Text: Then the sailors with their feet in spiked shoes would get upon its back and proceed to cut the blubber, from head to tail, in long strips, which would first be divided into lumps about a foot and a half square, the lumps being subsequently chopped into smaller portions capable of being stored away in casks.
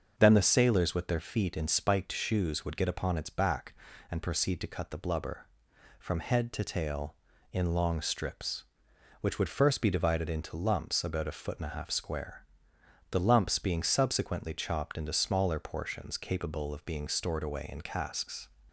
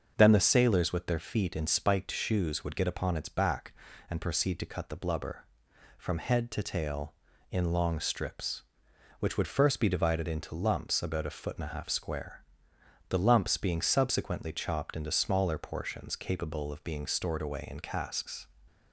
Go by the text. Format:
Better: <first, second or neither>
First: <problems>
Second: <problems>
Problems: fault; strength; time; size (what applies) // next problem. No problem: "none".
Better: neither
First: starts louder than the rest; until 1.1 s; 7 dB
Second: starts louder than the rest; until 1.1 s; 7 dB